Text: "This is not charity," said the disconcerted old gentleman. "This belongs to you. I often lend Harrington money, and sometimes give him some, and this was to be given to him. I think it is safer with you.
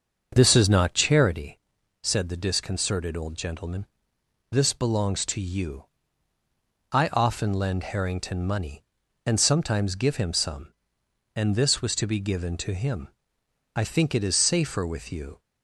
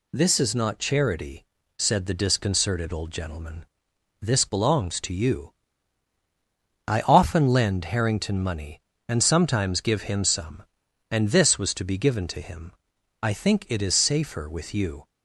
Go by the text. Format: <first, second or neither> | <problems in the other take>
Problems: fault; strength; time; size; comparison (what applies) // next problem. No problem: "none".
second | starts louder than the rest; until 1.4 s; 6.5 dB